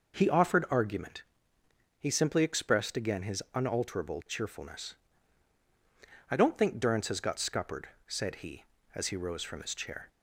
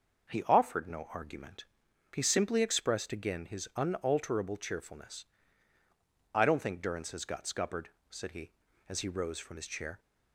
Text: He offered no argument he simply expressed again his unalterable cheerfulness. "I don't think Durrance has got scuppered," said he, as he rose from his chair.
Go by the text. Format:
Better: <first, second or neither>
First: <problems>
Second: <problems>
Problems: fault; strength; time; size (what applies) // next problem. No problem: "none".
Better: second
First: skips "no"; at 0.6 s // pauses between "argument" and "he"; noticeable; at 1.2 s; 0.74 s long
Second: pauses between "argument" and "he"; noticeable; at 1.6 s; 0.50 s long